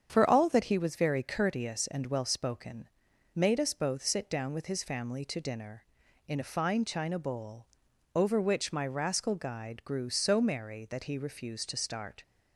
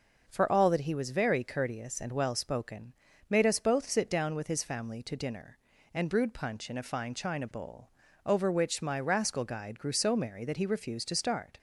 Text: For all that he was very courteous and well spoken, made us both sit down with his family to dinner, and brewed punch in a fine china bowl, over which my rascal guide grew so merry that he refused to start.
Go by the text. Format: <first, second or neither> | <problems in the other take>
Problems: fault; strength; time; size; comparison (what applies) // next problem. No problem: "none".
second | starts louder than the rest; strong; until 1.1 s; 7.5 dB // skips "and brewed punch"; at 6.0 s